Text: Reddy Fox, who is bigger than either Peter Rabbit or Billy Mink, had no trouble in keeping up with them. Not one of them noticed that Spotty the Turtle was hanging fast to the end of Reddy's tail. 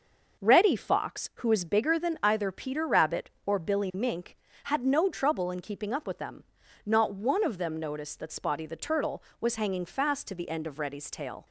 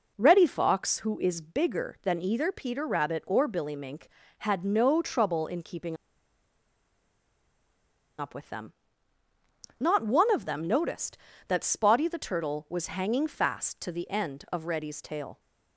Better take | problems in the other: first | pauses between "keeping" and "up"; strong; at 5.9 s; 2.2 s long

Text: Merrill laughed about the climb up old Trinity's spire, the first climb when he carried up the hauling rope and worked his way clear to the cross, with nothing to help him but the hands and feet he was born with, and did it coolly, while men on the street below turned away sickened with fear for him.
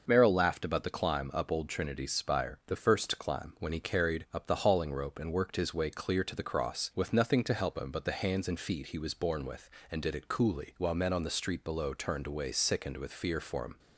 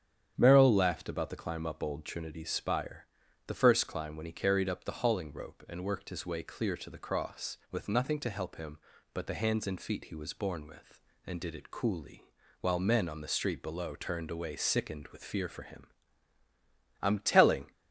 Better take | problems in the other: first | starts louder than the rest; strong; until 1.3 s; 8.5 dB // goes on to say "I'm telling"; noticeable; from 17.0 s on; 0.70 s long

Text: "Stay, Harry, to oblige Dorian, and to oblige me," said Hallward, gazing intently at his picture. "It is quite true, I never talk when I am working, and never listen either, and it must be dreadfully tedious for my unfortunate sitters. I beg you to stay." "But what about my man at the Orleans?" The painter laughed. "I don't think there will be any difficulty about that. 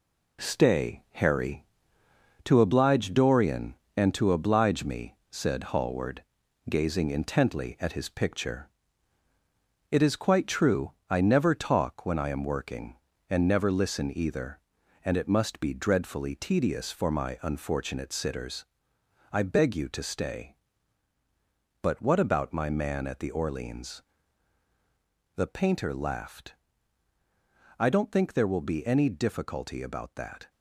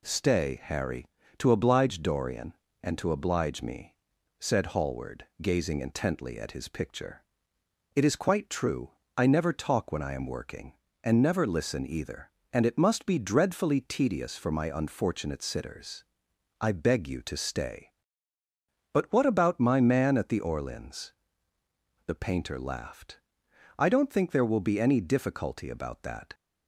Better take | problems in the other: second | gets quieter; throughout; 6.5 dB

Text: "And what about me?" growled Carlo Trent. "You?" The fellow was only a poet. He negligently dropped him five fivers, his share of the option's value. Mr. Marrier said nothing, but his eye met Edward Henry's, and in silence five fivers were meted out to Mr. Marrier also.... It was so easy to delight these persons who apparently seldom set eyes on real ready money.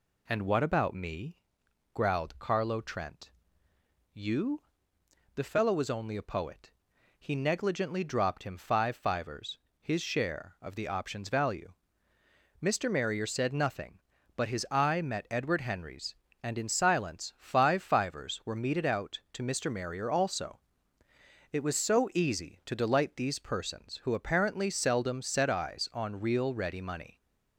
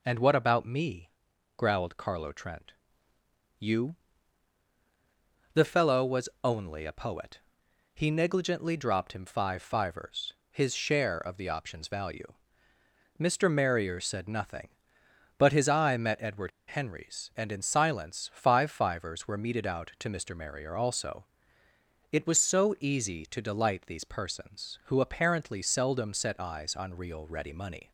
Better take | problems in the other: first | pauses between "Edward" and "Henry's"; slight; at 16.5 s; 0.19 s long

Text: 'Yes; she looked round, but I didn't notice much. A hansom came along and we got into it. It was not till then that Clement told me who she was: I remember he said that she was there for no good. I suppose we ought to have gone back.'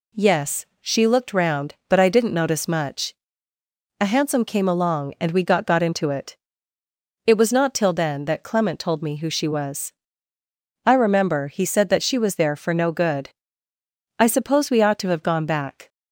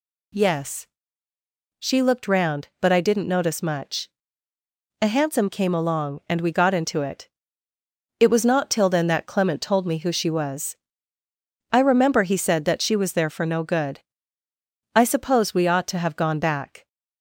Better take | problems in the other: second | says "got" twice; at 5.6 s

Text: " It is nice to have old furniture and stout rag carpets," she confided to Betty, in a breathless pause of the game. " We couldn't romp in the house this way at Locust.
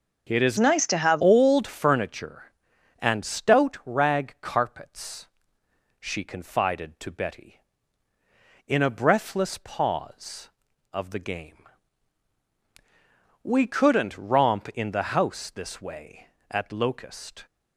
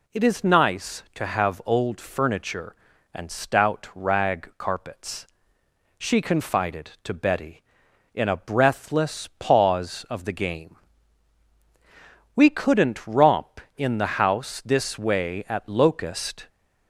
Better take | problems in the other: second | changes voice from "nice" to "have"; from 0.5 to 1.2 s; 0.7 s long

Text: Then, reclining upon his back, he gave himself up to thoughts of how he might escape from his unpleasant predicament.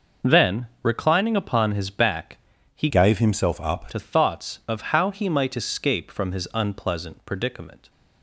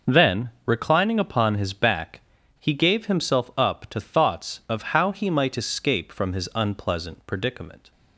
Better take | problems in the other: second | starts louder than the rest; noticeable; until 1.3 s; 6 dB; noticeable in the second // changes voice from "gave" to "up"; from 2.8 to 3.9 s; 1.1 s long

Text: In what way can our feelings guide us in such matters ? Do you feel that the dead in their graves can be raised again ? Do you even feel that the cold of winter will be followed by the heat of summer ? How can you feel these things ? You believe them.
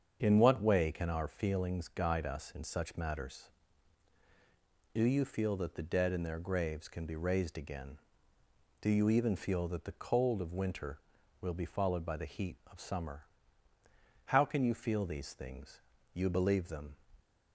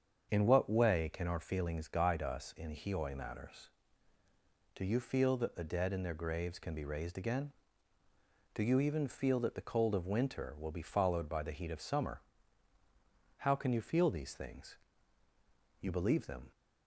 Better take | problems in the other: first | starts louder than the rest; until 1.3 s; 7 dB; strong in the first // says "hioi" for "such"; at 2.7 s

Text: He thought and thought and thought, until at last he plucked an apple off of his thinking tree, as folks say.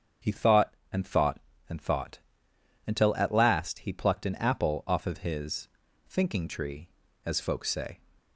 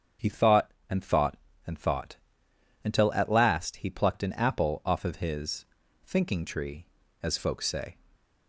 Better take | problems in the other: neither | starts louder than the rest; strong; the same in both // pauses between "his" and "thinking"; the same in both

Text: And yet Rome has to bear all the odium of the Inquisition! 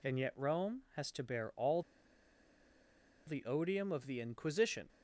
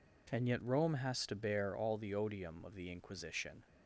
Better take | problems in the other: second | pauses between "all" and "the"; strong; at 1.8 s; 1.4 s long

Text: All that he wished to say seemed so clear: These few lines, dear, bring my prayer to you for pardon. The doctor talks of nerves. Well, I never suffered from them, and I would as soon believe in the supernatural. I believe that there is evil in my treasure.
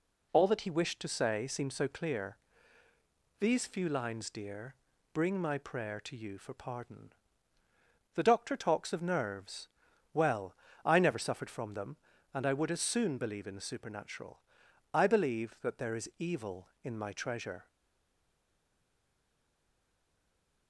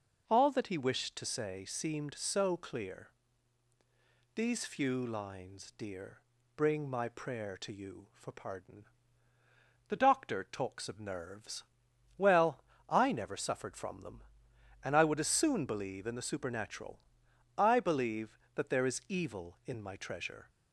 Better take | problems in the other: second | stays silent after the last word; strong; from 17.6 s on; 3.0 s long

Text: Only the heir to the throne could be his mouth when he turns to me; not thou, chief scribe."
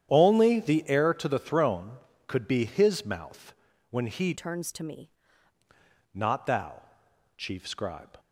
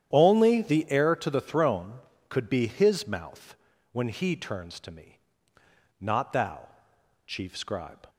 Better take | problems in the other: second | starts louder than the rest; strong; until 1.1 s; 10 dB; strong in the second // pauses between "mouth" and "when"; at 3.5 s; 0.38 s long; also in the second // changes voice from "turns" to "me"; from 4.3 to 5.1 s; 0.8 s long

